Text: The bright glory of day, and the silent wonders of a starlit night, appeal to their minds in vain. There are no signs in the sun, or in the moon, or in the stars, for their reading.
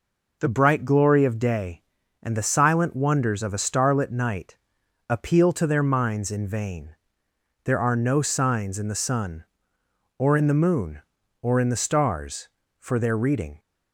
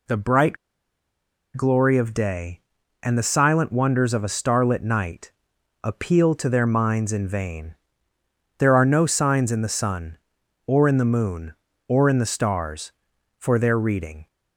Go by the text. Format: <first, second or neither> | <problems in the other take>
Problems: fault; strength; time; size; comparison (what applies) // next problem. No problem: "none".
first | pauses between "bright" and "glory"; at 0.5 s; 1.0 s long